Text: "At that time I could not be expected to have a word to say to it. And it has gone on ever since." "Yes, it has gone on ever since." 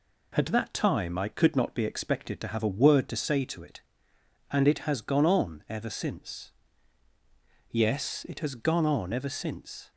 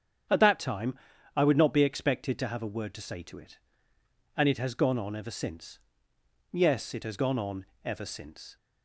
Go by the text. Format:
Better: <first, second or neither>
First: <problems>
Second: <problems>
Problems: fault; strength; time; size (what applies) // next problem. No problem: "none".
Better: first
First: none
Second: starts louder than the rest; strong; until 1.6 s; 8.5 dB // pauses between "time" and "I"; at 0.9 s; 0.38 s long // says "would" for "could"; at 1.4 s // pauses between "on" and "ever"; slight; at 7.6 s; 0.18 s long